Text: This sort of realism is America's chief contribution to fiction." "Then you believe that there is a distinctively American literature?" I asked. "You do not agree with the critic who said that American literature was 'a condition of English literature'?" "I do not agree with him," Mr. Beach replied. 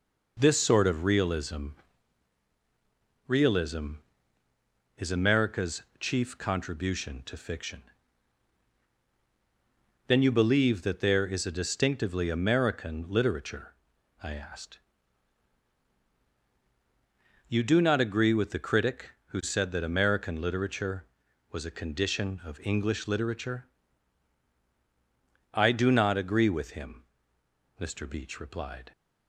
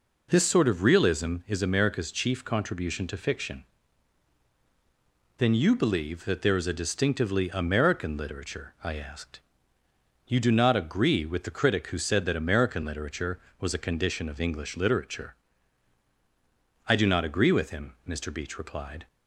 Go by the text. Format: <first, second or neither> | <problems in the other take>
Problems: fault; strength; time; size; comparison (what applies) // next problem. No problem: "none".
second | says "realism" twice; at 3.2 s // pauses between "America's" and "chief"; slight; at 5.8 s; 0.16 s long